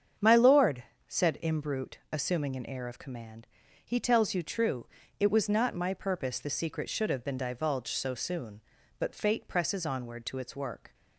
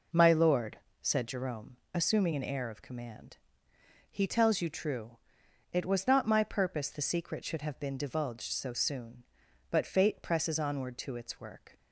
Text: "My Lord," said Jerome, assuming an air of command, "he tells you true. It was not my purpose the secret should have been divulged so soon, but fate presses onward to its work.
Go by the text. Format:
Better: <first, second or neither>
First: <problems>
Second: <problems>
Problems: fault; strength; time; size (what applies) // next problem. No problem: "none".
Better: second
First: starts louder than the rest; strong; until 1.4 s; 7.5 dB // says "Imbrute" for "Jerome"; at 1.4 s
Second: none